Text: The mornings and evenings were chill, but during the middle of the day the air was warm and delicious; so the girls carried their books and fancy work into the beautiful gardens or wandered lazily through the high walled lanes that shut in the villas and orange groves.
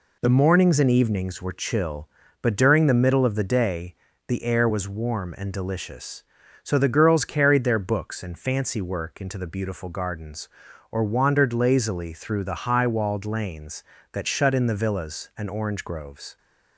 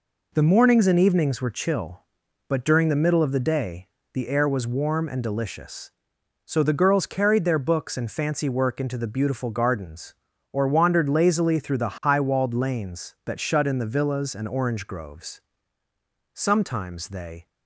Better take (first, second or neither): first